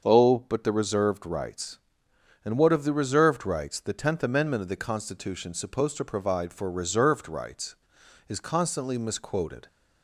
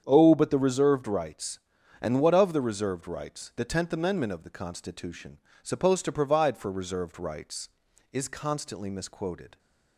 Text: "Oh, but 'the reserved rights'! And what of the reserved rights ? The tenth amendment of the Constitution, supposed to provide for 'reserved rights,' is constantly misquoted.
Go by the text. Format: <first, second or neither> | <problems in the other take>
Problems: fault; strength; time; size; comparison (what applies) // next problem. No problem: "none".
neither | starts louder than the rest; the same in both